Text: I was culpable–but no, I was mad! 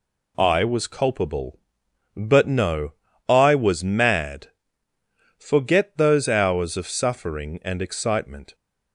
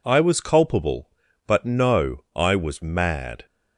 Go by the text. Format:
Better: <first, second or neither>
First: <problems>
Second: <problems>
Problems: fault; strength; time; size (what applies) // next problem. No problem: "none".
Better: second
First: goes on to say "Forget those hours of suffering and excitement"; strong; from 5.3 s on; 3.1 s long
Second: none